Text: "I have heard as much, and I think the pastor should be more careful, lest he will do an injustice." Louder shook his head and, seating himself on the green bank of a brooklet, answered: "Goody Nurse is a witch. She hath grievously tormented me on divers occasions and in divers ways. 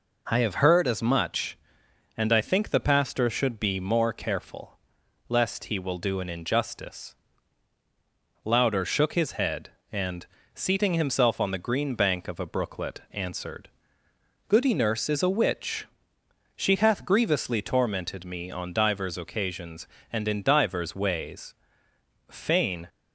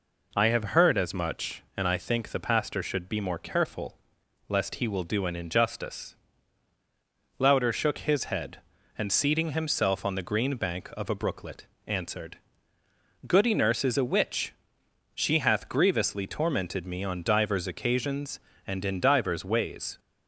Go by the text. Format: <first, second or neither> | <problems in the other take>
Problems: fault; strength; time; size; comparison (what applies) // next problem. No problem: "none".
second | goes on to say "Fain"; from 22.2 s on; 0.60 s long